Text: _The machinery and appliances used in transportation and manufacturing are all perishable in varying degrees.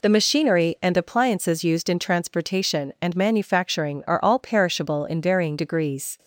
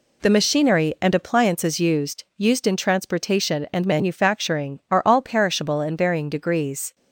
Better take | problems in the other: first | says "used" twice; at 2.3 s

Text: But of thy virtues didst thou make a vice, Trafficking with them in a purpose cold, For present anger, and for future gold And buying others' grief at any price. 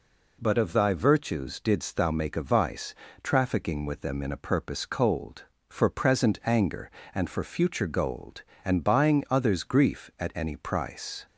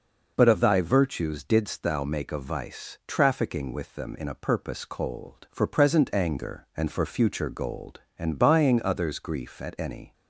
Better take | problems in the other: first | stops before "price"; at 10.1 s

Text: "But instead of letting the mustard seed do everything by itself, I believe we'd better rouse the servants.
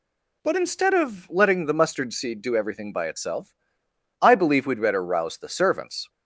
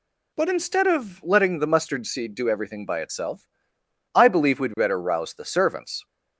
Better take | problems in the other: neither | none

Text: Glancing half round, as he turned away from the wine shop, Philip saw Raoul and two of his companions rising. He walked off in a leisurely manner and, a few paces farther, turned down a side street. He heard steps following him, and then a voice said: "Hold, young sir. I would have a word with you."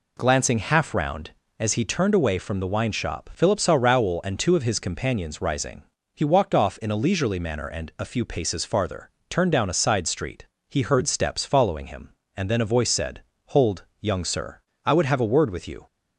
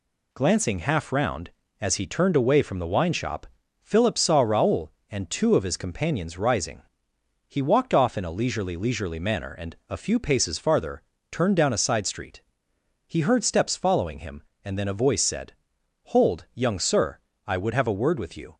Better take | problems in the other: first | says "leisurely" twice; at 8.7 s

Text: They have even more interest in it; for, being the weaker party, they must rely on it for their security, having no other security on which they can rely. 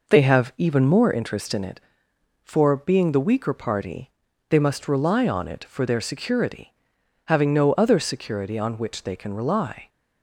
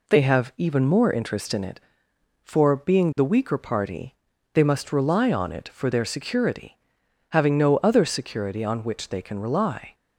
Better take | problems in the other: second | starts louder than the rest; noticeable; until 1.1 s; 5 dB

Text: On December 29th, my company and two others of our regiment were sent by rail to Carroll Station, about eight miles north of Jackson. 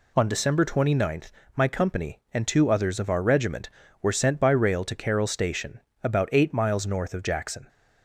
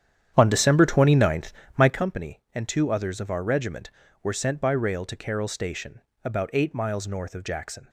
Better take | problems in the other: first | starts louder than the rest; strong; until 2.0 s; 9.5 dB

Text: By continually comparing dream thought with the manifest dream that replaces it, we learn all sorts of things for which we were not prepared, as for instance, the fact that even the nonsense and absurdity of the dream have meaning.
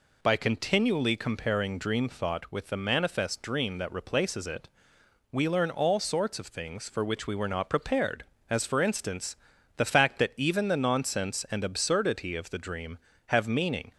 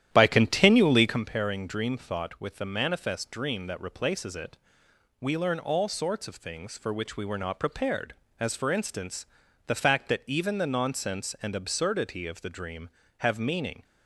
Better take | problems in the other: first | starts louder than the rest; strong; until 1.2 s; 11 dB

